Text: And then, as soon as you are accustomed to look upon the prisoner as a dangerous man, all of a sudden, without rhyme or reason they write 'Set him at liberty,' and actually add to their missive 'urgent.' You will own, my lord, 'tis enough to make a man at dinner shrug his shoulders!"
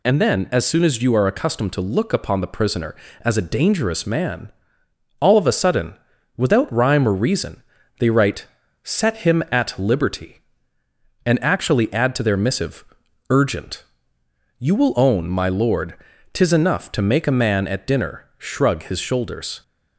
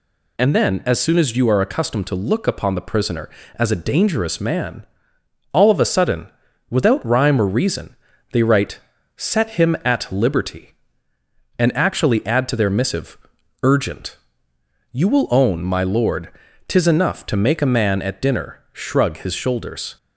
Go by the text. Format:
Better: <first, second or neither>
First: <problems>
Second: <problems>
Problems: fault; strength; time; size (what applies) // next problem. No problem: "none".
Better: neither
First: pauses between "reason" and "they"; slight; at 7.6 s; 0.36 s long // pauses between "write" and "Set"; slight; at 8.4 s; 0.36 s long // pauses between "missive" and "urgent"; at 12.8 s; 0.44 s long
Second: pauses between "reason" and "they"; slight; at 7.9 s; 0.36 s long // pauses between "write" and "Set"; slight; at 8.7 s; 0.36 s long // pauses between "missive" and "urgent"; at 13.1 s; 0.44 s long